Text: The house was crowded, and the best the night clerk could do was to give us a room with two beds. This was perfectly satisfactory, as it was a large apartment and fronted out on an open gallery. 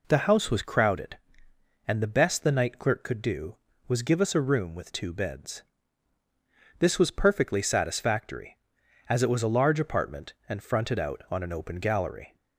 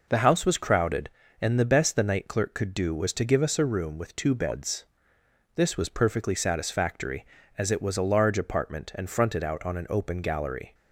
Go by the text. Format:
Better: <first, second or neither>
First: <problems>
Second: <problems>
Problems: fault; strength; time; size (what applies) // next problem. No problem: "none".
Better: second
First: skips "to"; at 4.0 s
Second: none